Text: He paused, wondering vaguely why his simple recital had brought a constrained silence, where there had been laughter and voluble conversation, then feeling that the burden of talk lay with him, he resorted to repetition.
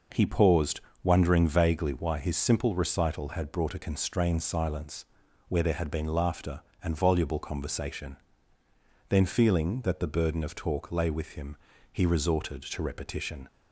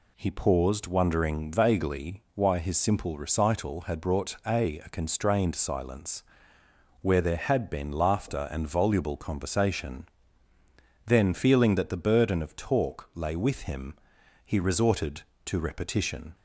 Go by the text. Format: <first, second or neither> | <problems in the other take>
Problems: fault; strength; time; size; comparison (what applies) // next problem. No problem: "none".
first | says "a" twice; at 4.7 s